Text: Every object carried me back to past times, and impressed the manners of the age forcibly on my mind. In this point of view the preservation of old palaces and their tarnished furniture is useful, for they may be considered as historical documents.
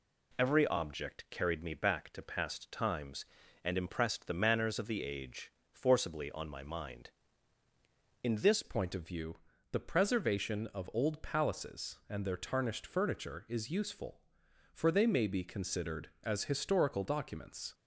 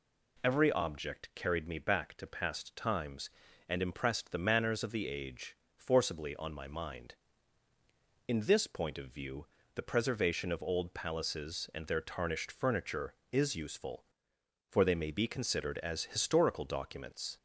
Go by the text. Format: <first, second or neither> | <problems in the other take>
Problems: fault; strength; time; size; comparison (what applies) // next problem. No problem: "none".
second | pauses between "age" and "forcibly"; slight; at 5.5 s; 0.22 s long; slight in the second // changes voice at "point"; from 8.6 s on; 9.1 s long // pauses between "view" and "the"; at 9.3 s; 0.38 s long; slight in the second